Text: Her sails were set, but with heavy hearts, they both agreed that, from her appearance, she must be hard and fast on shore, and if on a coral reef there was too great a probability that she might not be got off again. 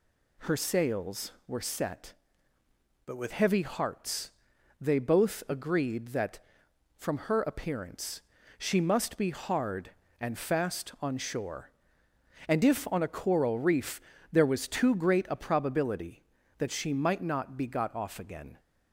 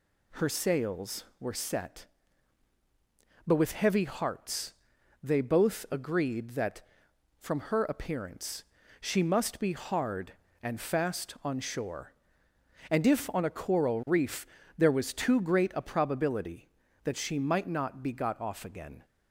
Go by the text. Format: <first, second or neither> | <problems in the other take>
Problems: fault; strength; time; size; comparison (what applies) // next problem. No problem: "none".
second | changes voice from "but" to "with"; from 3.0 to 3.3 s; 0.3 s long // pauses between "reef" and "there"; slight; at 13.9 s; 0.32 s long; slight in the second